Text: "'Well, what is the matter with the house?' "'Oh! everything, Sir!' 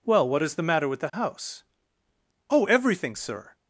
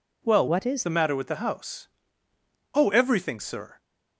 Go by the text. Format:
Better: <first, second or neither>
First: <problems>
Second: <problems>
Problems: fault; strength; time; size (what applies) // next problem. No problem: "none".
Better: first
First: none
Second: changes voice from "what" to "is"; from 0.4 to 0.8 s; 0.4 s long